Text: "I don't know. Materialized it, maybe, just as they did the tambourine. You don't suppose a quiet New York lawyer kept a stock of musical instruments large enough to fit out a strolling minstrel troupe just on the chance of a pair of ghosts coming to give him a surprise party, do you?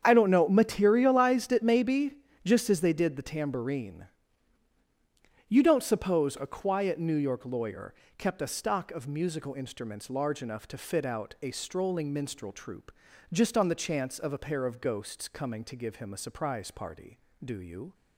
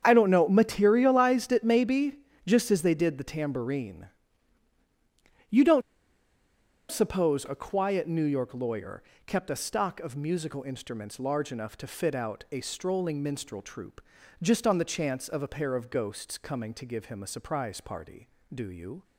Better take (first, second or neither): first